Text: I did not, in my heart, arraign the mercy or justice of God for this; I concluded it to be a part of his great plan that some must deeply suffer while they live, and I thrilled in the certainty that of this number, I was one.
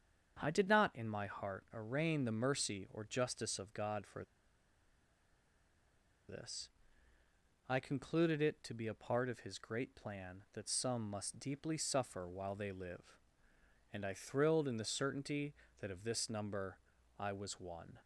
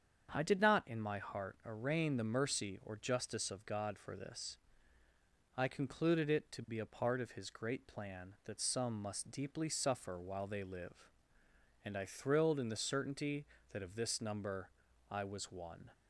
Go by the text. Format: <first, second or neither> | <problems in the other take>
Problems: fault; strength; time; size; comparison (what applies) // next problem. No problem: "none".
second | starts louder than the rest; strong; until 1.4 s; 7.5 dB; strong in the second // pauses between "for" and "this"; strong; at 4.2 s; 2.0 s long